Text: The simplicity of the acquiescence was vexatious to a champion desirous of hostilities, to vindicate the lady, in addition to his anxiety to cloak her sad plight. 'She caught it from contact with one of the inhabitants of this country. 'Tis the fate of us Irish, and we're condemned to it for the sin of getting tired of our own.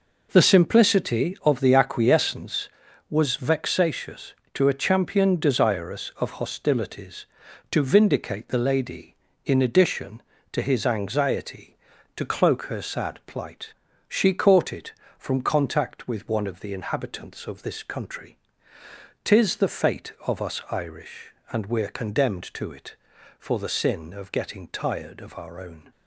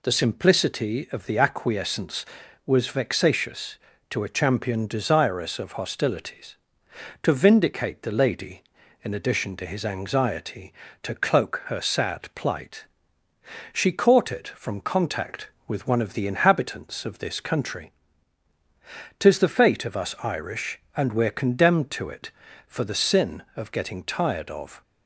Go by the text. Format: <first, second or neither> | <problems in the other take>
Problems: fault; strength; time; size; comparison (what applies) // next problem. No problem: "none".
first | stops before "our own"; at 24.8 s